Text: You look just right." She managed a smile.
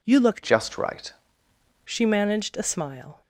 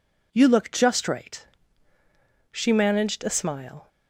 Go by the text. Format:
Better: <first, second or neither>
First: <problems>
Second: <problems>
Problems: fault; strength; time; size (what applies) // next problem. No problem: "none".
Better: second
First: changes voice from "just" to "right"; from 0.4 to 1.1 s; 0.7 s long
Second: none